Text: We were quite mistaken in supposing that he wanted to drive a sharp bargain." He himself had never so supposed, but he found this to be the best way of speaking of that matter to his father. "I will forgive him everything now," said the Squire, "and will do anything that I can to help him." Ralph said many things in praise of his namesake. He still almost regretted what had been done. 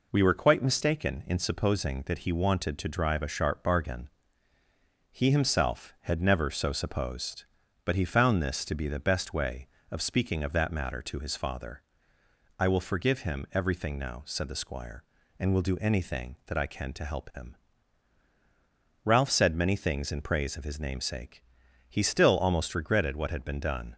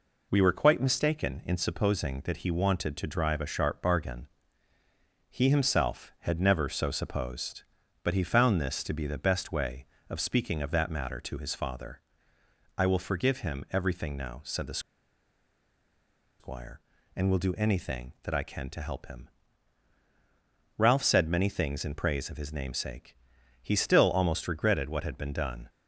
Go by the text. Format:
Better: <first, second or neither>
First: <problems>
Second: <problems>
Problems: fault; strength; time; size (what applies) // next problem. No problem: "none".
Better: first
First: none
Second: pauses between "the" and "Squire"; strong; at 14.7 s; 1.6 s long